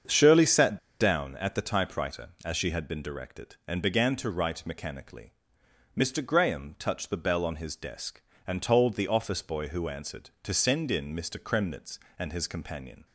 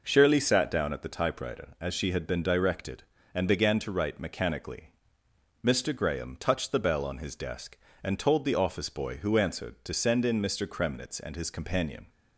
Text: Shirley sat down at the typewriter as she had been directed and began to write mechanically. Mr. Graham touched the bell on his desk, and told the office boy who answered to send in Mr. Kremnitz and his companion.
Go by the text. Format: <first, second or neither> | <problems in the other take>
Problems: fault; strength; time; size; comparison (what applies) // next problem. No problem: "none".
second | starts louder than the rest; strong; until 1.3 s; 7 dB // pauses between "sat" and "down"; slight; at 0.7 s; 0.22 s long